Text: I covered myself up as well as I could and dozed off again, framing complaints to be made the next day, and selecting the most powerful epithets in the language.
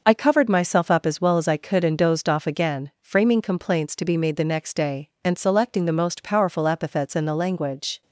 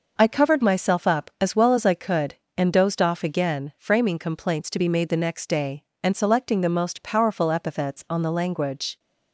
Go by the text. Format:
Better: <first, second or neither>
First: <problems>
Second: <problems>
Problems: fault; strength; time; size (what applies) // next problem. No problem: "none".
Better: first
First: none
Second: says "on" for "in"; at 8.1 s